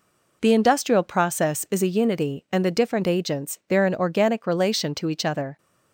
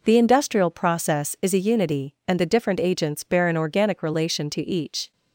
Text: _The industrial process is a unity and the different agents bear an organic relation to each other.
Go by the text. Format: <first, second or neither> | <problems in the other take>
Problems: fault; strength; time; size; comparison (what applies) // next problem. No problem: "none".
first | stops before "other"; at 5.1 s